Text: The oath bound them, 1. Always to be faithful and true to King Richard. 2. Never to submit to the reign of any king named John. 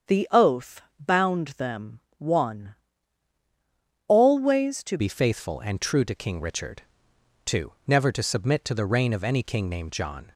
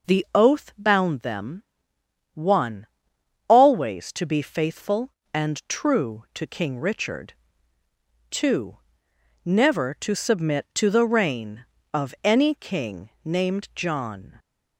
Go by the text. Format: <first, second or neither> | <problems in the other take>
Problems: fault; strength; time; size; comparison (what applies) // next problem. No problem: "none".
second | starts louder than the rest; strong; until 1.3 s; 7.5 dB // pauses between "oath" and "bound"; slight; at 0.8 s; 0.18 s long // changes voice at "be"; from 4.9 s on; 5.4 s long